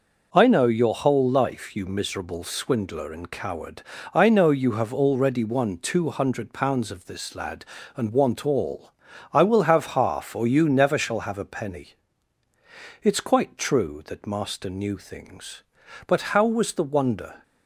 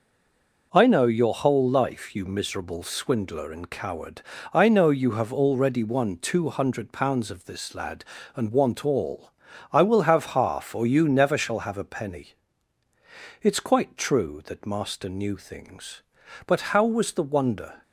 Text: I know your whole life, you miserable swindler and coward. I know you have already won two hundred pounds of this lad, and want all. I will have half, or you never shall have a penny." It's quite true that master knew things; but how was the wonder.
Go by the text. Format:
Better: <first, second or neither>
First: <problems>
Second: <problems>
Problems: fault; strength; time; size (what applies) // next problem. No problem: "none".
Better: first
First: none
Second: stays silent before the first word; slight; until 0.7 s; 0.7 s long